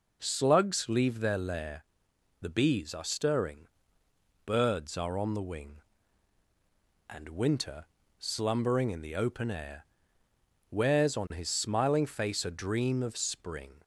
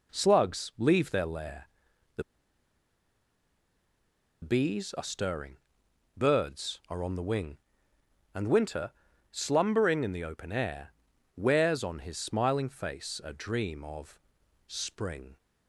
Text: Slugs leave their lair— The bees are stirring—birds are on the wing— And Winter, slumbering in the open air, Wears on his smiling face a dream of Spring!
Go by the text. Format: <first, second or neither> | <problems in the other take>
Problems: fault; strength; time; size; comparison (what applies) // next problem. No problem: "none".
first | pauses between "The" and "bees"; strong; at 2.2 s; 2.1 s long // pauses between "of" and "Spring"; noticeable; at 14.1 s; 0.48 s long